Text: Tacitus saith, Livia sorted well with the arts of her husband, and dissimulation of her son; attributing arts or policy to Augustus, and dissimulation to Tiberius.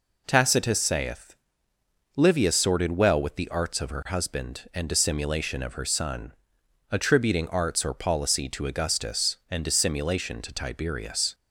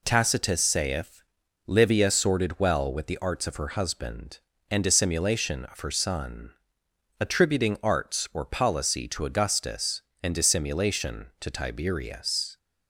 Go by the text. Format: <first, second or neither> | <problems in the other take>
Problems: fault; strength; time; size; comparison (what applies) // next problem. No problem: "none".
neither | none